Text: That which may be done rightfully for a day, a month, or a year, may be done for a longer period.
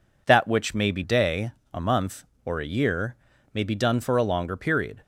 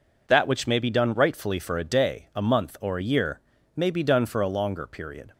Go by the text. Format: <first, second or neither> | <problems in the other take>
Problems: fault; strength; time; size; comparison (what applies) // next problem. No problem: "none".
second | skips "done rightfully for a"; at 1.0 s